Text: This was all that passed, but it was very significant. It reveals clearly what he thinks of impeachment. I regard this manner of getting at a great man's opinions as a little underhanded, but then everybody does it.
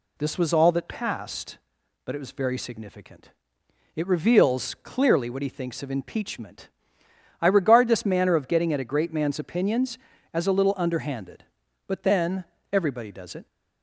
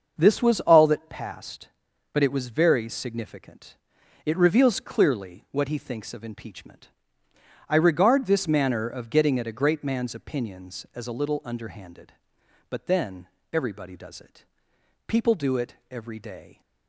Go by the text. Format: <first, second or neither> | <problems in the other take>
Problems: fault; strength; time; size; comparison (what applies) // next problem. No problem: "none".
first | starts louder than the rest; until 1.1 s; 6.5 dB // pauses between "then" and "everybody"; slight; at 13.2 s; 0.26 s long; slight in the first // goes on to say "People do it every day"; from 15.0 s on; 1.5 s long